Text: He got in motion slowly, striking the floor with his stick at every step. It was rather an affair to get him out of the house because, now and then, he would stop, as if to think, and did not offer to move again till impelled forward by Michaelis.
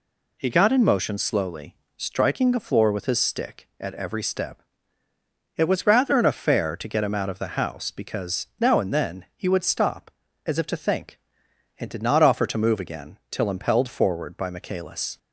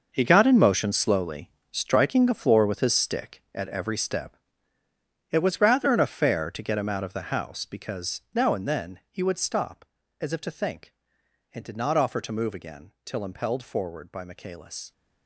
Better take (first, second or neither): first